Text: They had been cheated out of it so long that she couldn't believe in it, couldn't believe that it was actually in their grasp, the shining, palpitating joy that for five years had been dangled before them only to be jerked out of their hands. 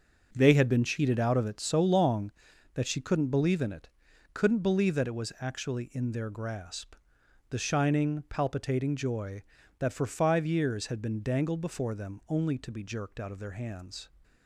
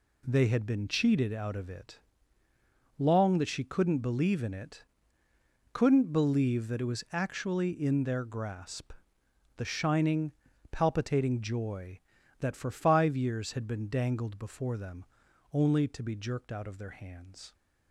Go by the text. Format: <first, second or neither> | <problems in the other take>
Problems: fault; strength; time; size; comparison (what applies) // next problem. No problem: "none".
first | skips "so"; at 2.4 s // pauses between "them" and "only"; noticeable; at 15.0 s; 0.48 s long